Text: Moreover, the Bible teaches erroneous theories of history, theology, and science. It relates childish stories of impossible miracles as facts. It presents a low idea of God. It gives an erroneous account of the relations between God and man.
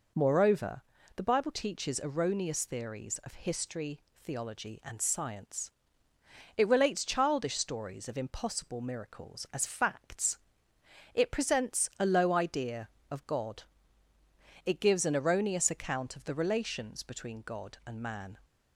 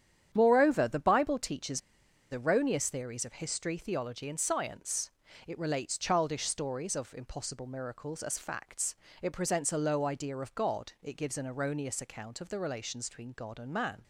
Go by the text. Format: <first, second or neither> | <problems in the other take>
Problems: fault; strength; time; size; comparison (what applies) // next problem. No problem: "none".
first | starts louder than the rest; strong; until 1.3 s; 9.5 dB // pauses between "teaches" and "erroneous"; noticeable; at 1.8 s; 0.52 s long